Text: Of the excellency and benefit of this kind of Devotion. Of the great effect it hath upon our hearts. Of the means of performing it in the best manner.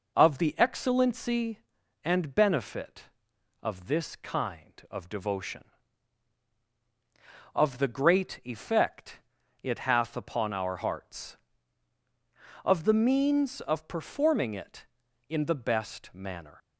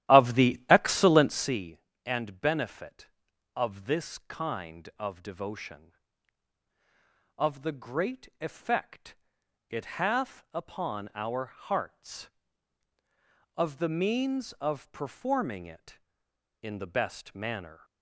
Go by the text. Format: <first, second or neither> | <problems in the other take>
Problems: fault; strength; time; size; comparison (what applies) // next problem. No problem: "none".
first | starts louder than the rest; strong; until 1.6 s; 13 dB // pauses between "effect" and "it"; noticeable; at 9.1 s; 0.54 s long; also in the first